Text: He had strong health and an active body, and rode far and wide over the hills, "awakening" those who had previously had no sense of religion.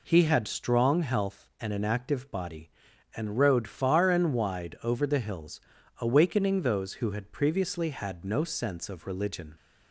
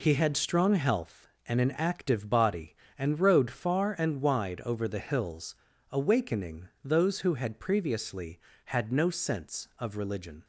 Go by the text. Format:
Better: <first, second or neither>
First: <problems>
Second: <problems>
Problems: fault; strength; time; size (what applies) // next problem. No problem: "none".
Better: neither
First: none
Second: none